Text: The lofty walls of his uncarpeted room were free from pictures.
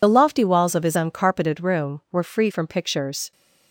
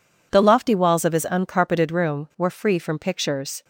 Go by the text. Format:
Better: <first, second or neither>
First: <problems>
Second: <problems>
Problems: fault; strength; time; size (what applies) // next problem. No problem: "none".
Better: second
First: loses the start of "The"; at 0.0 s; 35 ms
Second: none